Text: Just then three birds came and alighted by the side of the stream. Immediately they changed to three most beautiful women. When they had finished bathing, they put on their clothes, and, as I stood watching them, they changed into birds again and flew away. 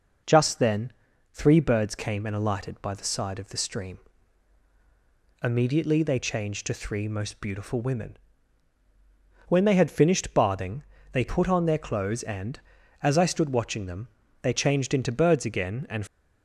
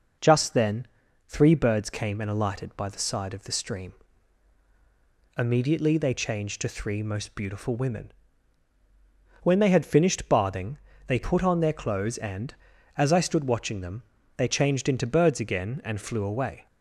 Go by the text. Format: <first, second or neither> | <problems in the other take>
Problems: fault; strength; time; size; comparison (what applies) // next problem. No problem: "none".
second | pauses between "then" and "three"; at 0.9 s; 0.42 s long; also in the second // stops before "flew away"; at 16.0 s